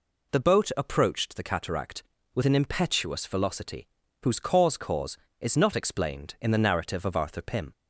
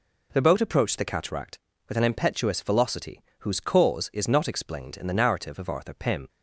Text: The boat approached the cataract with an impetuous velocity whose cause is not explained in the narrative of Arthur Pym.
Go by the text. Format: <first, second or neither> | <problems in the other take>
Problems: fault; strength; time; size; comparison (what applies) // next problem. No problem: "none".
second | pauses between "velocity" and "whose"; slight; at 3.8 s; 0.36 s long; slight in the second // says "cause" twice; at 4.7 s